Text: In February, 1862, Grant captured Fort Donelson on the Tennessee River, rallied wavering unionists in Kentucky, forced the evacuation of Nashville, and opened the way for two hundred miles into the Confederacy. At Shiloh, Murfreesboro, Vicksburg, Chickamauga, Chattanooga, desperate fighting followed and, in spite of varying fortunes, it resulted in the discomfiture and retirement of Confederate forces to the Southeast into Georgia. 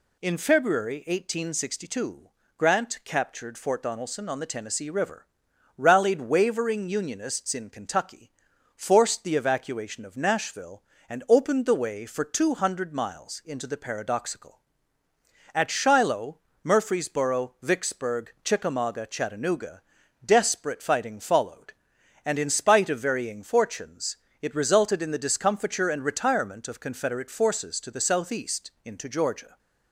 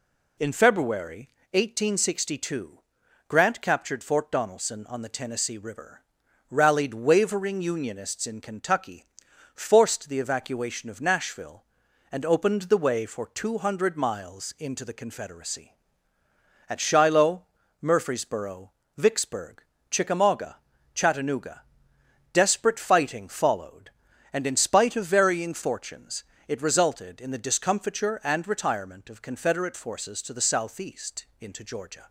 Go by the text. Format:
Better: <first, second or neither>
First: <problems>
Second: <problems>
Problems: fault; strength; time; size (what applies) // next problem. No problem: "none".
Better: second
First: says "Paradoxical" for "Confederacy"; at 13.7 s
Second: none